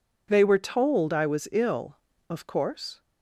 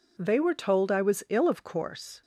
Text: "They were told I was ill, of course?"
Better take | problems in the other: neither | none

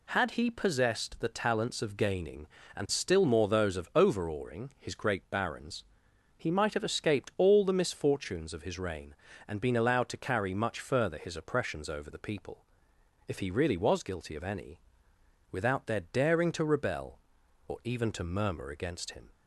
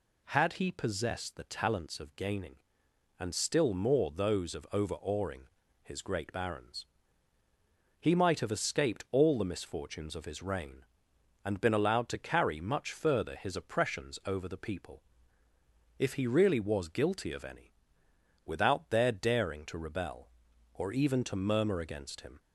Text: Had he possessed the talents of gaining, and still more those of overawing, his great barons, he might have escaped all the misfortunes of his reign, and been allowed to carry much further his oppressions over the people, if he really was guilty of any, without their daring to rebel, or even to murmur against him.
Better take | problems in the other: neither | none

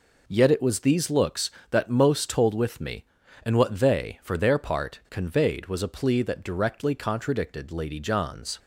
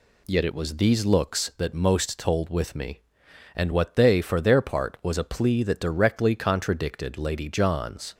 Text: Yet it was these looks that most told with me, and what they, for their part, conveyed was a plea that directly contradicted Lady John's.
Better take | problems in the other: first | skips "conveyed"; at 4.9 s

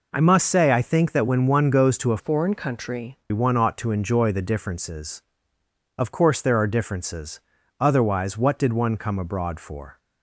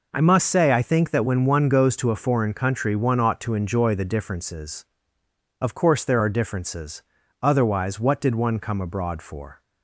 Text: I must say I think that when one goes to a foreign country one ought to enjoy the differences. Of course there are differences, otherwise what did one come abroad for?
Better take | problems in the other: second | changes voice from "foreign" to "country"; from 2.1 to 3.1 s; 1.0 s long

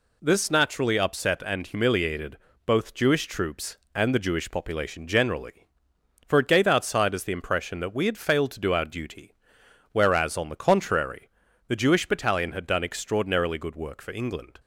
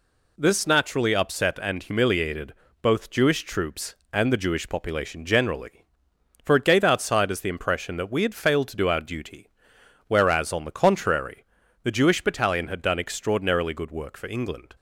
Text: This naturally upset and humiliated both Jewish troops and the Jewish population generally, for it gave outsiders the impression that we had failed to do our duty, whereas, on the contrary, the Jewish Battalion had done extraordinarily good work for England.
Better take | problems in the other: neither | pauses between "humiliated" and "both"; slight; the same in both

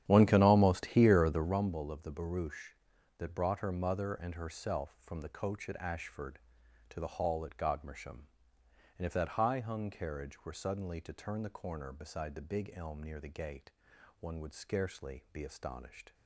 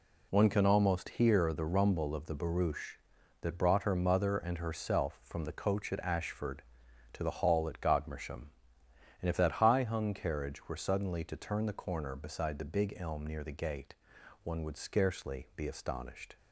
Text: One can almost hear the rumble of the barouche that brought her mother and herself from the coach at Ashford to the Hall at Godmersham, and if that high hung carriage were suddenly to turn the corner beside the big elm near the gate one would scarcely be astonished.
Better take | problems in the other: second | starts louder than the rest; strong; until 1.6 s; 10.5 dB // pauses between "gate" and "one"; noticeable; at 13.6 s; 0.50 s long; noticeable in the second

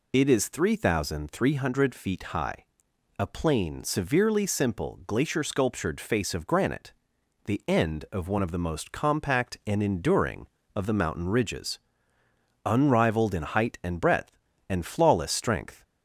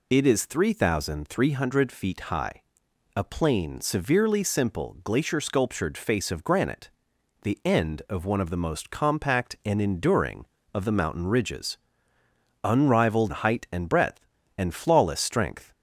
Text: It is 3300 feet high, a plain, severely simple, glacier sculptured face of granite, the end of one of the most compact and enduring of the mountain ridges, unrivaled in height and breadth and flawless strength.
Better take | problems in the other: first | skips "in"; at 13.3 s

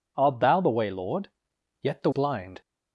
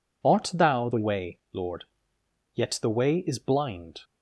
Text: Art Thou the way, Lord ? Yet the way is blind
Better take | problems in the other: second | skips "way is"; at 2.1 s

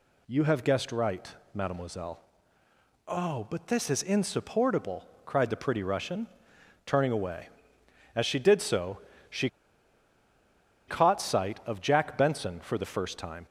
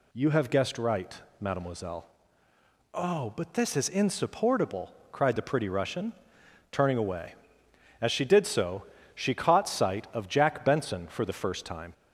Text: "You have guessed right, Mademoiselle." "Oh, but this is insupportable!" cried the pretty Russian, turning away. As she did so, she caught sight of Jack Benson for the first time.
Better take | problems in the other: second | pauses between "she" and "caught"; strong; at 9.4 s; 1.3 s long

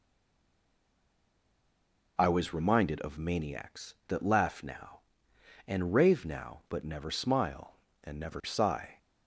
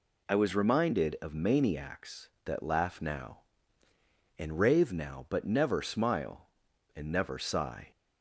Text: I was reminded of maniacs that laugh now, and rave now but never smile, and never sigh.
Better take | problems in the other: second | stays silent before the first word; until 2.1 s; 2.1 s long

